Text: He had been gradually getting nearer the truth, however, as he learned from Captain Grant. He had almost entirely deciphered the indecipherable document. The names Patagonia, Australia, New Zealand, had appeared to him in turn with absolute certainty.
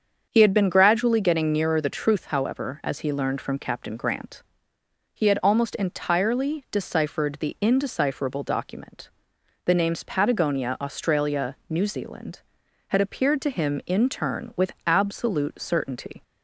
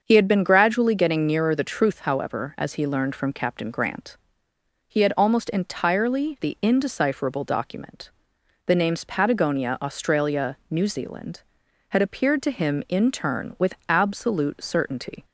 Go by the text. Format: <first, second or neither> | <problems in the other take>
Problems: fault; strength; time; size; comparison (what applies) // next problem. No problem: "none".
first | starts louder than the rest; until 1.0 s; 6.5 dB; also in the first // skips "deciphered"; at 6.3 s